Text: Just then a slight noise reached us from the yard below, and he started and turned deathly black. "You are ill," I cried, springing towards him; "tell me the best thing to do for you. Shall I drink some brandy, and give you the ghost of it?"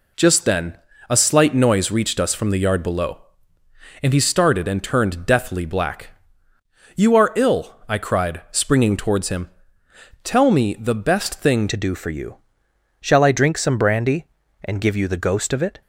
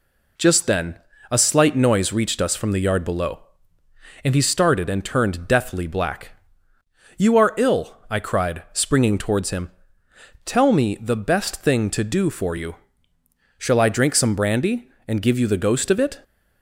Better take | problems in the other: second | pauses between "then" and "a"; slight; at 0.7 s; 0.34 s long; slight in the second // changes voice at "to"; from 11.6 s on; 4.2 s long

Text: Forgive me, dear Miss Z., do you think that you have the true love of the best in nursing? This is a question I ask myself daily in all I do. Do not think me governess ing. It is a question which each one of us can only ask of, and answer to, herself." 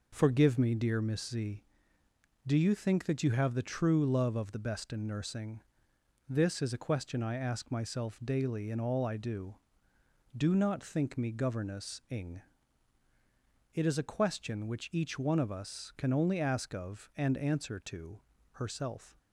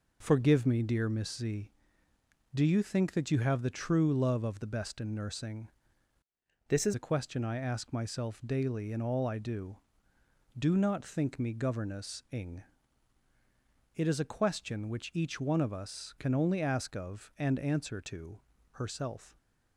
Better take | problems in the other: first | changes voice from "This" to "is"; from 6.6 to 6.9 s; 0.3 s long

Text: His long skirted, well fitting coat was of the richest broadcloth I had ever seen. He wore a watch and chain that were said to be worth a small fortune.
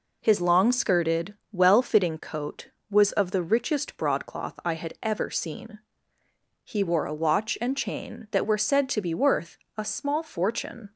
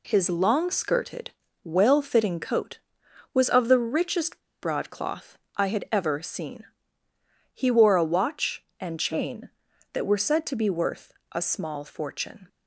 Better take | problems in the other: first | pauses between "richest" and "broadcloth"; slight; at 4.3 s; 0.21 s long // pauses between "broadcloth" and "I"; slight; at 5.3 s; 0.18 s long // pauses between "worth" and "a"; slight; at 11.1 s; 0.18 s long; slight in the first

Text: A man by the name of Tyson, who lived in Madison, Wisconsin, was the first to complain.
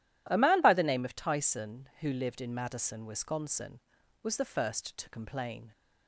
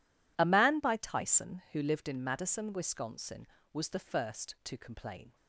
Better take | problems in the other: first | skips "the name of"; at 0.9 s

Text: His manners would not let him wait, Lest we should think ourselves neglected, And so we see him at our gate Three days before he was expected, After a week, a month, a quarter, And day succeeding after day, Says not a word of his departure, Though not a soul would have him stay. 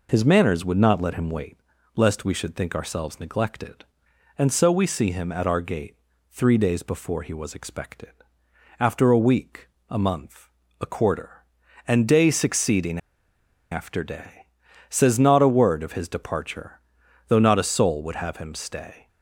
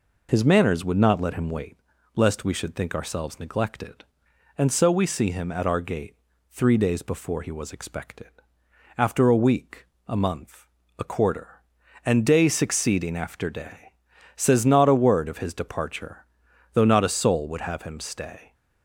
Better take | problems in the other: second | pauses between "gate" and "Three"; at 5.9 s; 0.38 s long; also in the second // pauses between "succeeding" and "after"; noticeable; at 12.9 s; 0.73 s long

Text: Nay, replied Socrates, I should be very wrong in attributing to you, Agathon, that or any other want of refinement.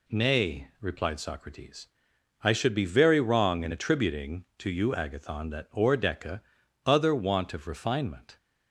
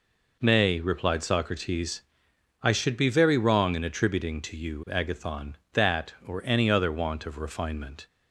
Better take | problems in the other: second | says "deca" for "any"; at 5.9 s

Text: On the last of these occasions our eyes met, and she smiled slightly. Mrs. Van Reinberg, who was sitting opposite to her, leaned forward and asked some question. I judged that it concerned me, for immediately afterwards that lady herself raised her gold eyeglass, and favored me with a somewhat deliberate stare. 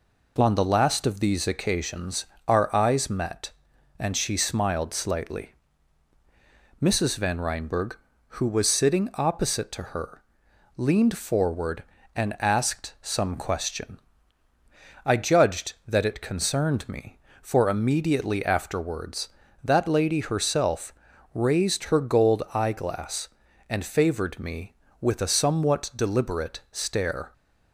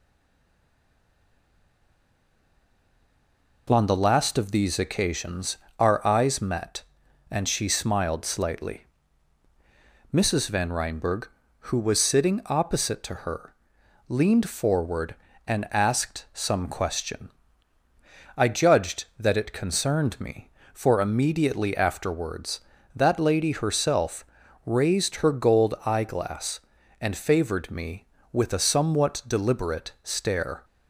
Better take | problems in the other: first | stays silent before the first word; strong; until 3.6 s; 3.6 s long // pauses between "occasions" and "our"; slight; at 5.5 s; 0.20 s long; slight in the first // pauses between "herself" and "raised"; at 24.2 s; 0.40 s long; also in the first

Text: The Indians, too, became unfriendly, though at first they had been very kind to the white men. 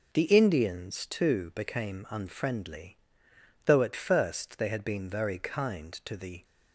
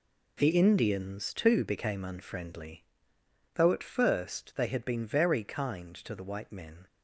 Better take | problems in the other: second | stops before "white men"; at 6.4 s

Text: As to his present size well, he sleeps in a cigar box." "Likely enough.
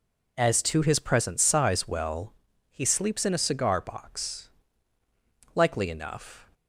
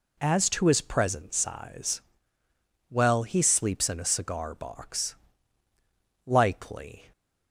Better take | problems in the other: first | pauses between "size" and "well"; noticeable; at 2.0 s; 0.88 s long // stops before "enough"; at 7.1 s

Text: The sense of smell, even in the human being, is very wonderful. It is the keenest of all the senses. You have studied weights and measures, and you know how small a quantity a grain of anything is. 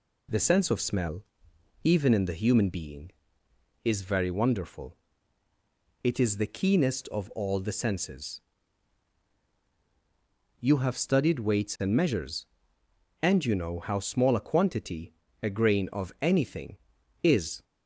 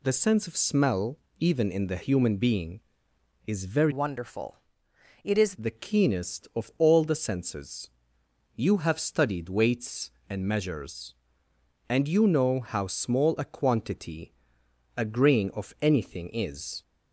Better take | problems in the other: first | changes voice from "wonderful" to "is"; from 3.9 to 5.5 s; 1.6 s long // pauses between "quantity" and "a"; noticeable; at 14.3 s; 0.66 s long; slight in the first

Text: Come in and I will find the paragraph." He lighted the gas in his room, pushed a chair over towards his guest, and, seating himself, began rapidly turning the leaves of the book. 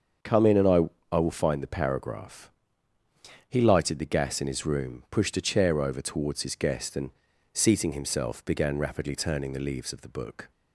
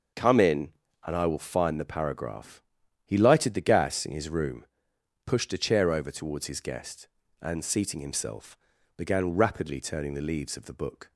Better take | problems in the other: second | starts louder than the rest; strong; until 1.5 s; 7 dB; noticeable in the second // says "I" twice; at 1.1 s

